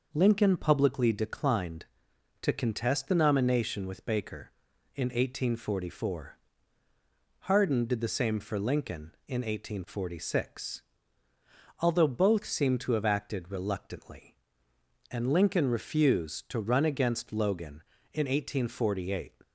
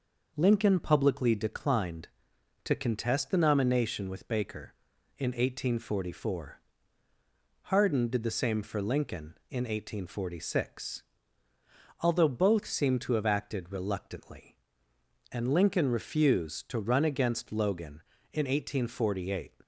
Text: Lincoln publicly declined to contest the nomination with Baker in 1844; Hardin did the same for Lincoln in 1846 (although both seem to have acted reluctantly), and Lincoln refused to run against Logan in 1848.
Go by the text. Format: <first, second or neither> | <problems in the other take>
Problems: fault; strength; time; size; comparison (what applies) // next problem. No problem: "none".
neither | none